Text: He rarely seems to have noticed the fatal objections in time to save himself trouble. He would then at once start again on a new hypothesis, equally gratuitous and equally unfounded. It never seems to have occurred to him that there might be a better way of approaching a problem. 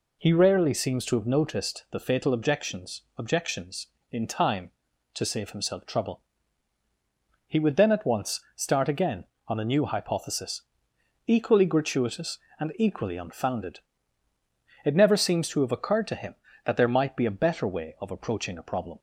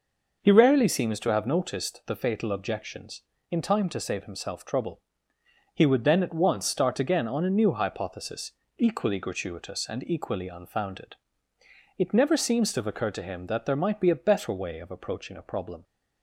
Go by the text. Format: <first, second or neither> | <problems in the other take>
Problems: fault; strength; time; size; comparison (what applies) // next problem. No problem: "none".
second | says "objections" twice; at 3.1 s // pauses between "once" and "start"; slight; at 8.4 s; 0.16 s long